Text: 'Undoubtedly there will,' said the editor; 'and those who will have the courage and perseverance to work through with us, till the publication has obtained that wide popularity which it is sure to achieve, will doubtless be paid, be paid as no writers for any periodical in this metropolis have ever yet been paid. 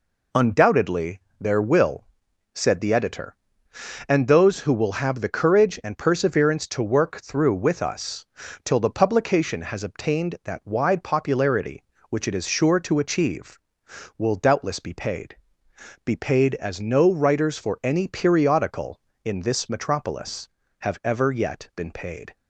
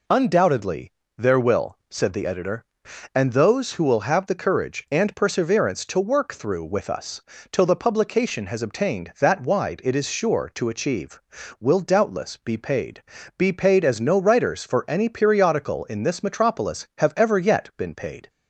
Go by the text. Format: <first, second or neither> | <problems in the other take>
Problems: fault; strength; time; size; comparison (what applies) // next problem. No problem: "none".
first | pauses between "Undoubtedly" and "there"; slight; at 0.9 s; 0.26 s long; slight in the first // skips "popularity which"; at 9.8 s